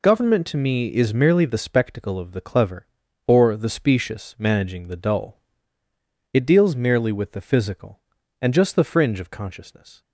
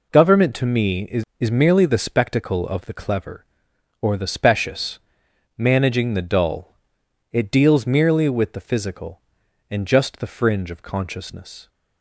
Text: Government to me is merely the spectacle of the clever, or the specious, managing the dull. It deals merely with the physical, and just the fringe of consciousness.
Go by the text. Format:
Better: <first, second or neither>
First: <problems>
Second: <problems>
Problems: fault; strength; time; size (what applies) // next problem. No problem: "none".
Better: first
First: none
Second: says "is" twice; at 1.3 s